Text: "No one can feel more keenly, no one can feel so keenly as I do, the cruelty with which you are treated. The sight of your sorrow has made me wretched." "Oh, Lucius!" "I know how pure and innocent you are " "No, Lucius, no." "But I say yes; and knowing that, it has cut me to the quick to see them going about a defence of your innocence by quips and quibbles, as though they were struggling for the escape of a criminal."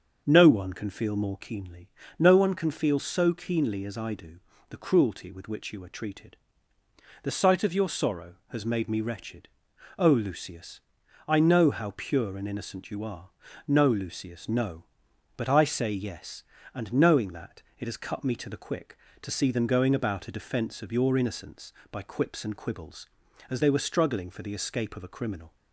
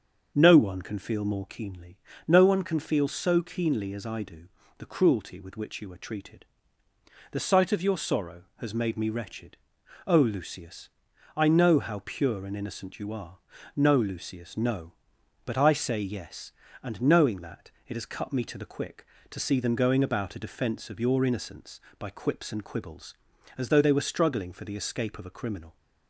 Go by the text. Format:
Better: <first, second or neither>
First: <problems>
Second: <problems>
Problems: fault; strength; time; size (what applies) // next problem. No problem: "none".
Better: second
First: starts louder than the rest; until 1.2 s; 6.5 dB // skips "though"; at 23.6 s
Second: starts louder than the rest; until 1.3 s; 6.5 dB